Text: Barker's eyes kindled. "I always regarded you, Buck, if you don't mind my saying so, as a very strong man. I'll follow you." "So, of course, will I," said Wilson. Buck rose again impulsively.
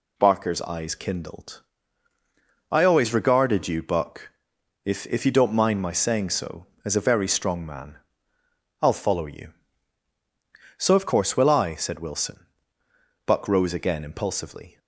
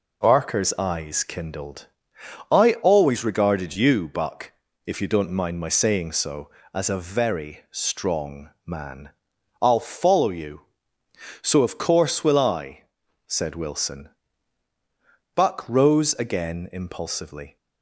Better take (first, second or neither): second